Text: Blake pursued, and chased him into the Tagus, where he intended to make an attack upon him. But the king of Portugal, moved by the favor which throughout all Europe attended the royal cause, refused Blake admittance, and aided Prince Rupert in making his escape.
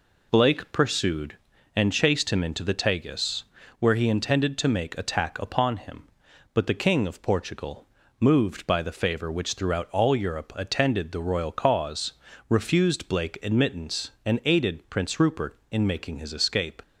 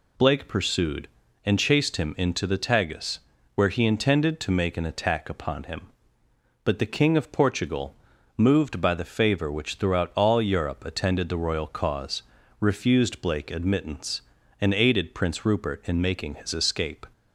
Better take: second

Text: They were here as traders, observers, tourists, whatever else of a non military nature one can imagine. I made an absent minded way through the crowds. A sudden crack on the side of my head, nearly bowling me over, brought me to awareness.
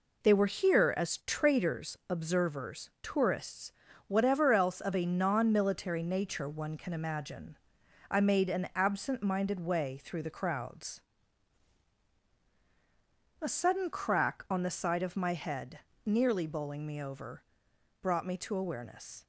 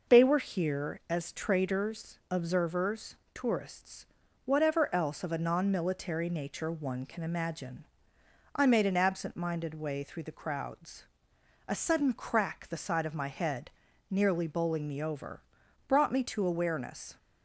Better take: first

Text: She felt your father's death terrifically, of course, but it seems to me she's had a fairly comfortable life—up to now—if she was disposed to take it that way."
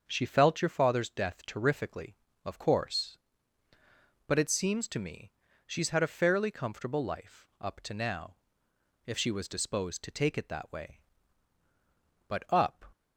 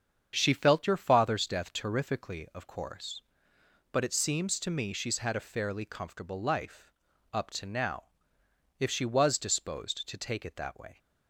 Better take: second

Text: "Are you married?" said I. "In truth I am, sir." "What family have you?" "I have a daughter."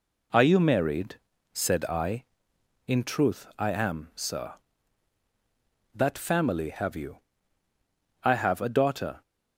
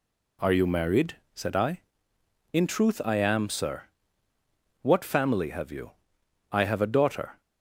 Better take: second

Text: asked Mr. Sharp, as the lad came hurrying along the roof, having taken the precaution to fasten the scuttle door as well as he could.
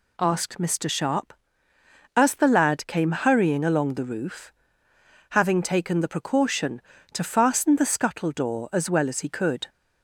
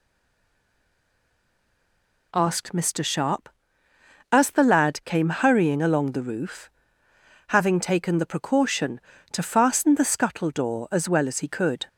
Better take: first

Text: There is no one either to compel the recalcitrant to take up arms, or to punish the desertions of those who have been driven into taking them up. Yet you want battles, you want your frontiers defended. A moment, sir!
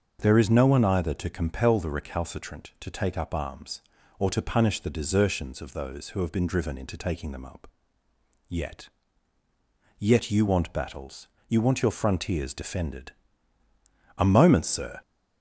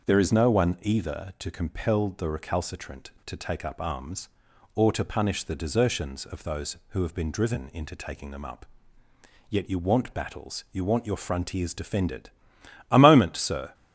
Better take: second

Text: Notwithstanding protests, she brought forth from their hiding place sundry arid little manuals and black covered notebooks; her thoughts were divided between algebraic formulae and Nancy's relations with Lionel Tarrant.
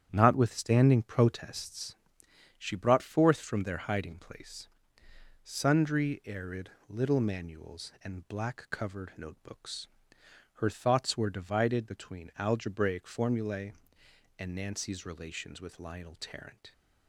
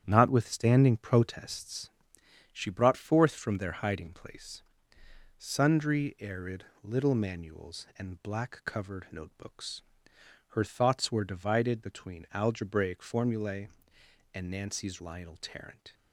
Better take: first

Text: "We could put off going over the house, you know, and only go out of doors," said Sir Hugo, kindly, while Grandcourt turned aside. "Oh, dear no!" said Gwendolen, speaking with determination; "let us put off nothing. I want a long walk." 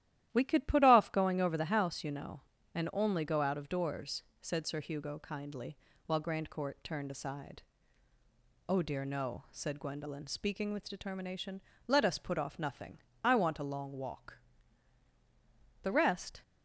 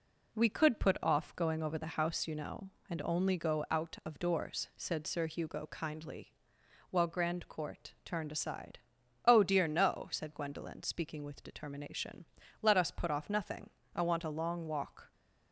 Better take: second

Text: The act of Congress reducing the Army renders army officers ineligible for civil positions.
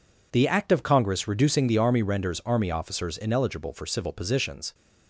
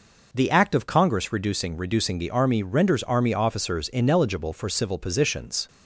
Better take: first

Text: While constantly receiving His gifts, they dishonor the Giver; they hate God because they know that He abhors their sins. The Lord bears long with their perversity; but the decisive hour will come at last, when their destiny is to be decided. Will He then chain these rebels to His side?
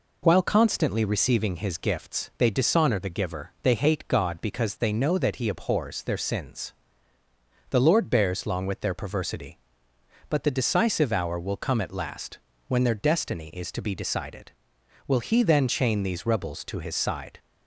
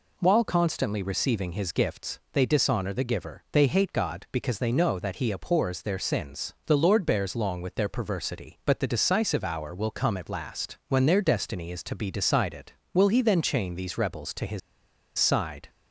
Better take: first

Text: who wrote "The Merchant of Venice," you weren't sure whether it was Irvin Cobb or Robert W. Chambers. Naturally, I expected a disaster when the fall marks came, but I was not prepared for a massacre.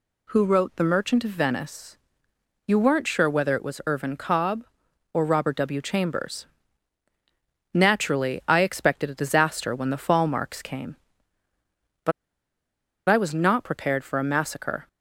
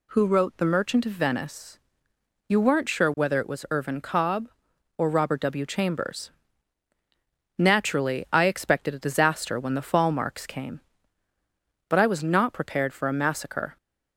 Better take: second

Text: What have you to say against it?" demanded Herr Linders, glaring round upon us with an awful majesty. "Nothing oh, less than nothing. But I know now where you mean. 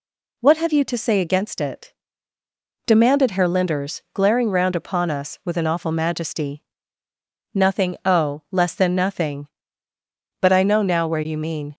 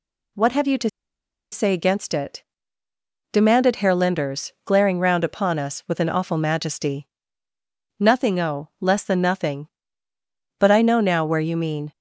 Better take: first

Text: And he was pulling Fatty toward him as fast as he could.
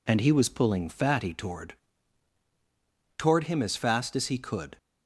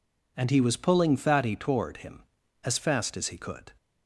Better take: second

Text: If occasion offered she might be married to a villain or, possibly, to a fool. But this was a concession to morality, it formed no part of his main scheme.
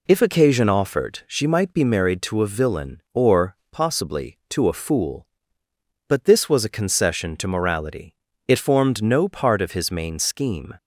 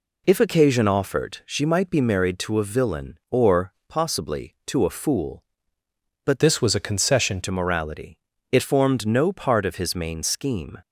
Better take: first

